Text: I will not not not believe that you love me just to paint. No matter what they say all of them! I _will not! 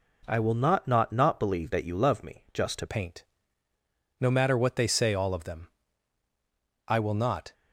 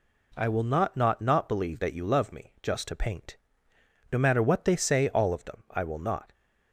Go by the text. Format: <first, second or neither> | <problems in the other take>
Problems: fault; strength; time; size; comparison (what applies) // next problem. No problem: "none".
second | changes voice at "paint"; from 2.8 s on; 4.7 s long